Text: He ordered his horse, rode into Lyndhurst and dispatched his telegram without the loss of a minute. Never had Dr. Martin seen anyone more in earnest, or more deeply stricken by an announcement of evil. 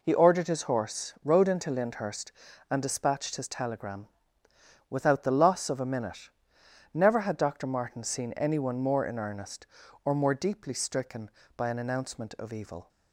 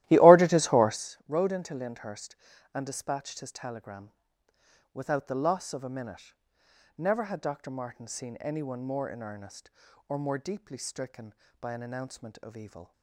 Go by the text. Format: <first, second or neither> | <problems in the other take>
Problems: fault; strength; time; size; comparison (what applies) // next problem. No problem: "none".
first | starts louder than the rest; strong; until 1.0 s; 15 dB // pauses between "telegram" and "without"; noticeable; at 4.1 s; 0.82 s long; noticeable in the first